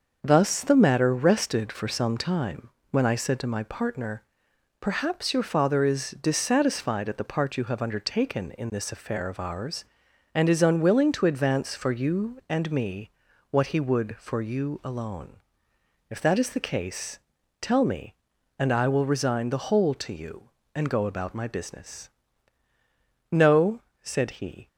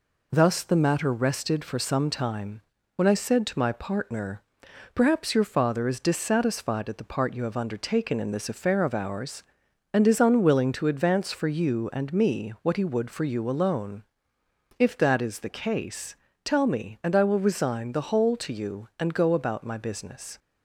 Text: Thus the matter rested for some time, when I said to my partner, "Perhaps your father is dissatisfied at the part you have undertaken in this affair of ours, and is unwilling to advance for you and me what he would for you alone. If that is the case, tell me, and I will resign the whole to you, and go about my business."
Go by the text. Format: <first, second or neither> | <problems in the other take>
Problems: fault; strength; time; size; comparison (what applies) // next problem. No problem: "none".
second | starts louder than the rest; until 1.2 s; 6 dB // pauses between "me" and "what"; at 13.1 s; 0.40 s long // goes on to say "No said he"; from 23.3 s on; 1.3 s long